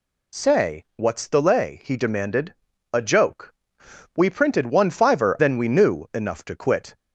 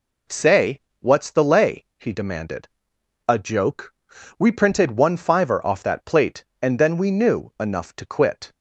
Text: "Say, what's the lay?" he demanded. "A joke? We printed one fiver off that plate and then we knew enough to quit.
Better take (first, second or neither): second